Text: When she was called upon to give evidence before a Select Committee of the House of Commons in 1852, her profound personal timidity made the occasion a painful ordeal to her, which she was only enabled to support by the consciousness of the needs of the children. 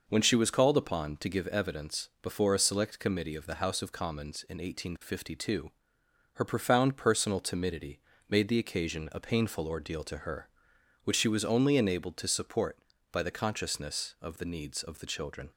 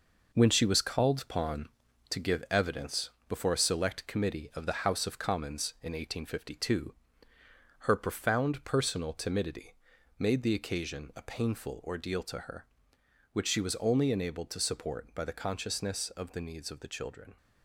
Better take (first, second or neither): first